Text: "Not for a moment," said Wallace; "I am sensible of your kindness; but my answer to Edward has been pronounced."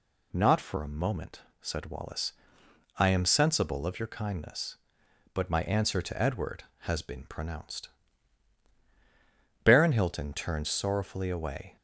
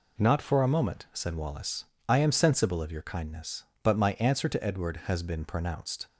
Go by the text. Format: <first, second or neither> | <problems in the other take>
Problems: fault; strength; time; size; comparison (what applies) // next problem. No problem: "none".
second | goes on to say "Baron Hilton turned sorrowfully away"; strong; from 9.6 s on; 2.1 s long